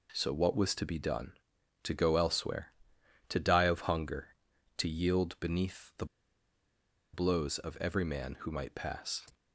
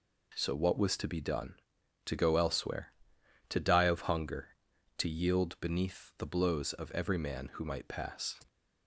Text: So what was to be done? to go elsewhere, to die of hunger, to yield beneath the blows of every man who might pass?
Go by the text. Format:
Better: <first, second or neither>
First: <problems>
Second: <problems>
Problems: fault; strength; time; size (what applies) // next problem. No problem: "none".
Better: second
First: pauses between "the" and "blows"; at 6.0 s; 1.0 s long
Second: none